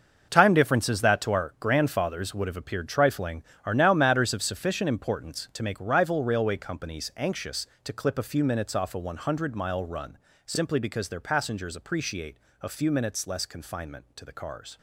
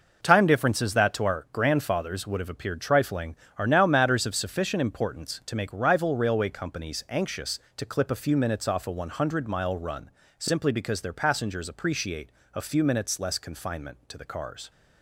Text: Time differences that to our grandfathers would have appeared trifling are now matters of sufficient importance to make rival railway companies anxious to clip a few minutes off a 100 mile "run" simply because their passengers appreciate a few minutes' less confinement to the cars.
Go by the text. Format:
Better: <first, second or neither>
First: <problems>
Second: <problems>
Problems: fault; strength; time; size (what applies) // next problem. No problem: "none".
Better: second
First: gets quieter; strong; throughout; 11.5 dB // pauses between "run" and "simply"; slight; at 10.1 s; 0.28 s long // pauses between "appreciate" and "a"; slight; at 12.3 s; 0.24 s long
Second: pauses between "run" and "simply"; slight; at 10.0 s; 0.28 s long // pauses between "appreciate" and "a"; slight; at 12.2 s; 0.24 s long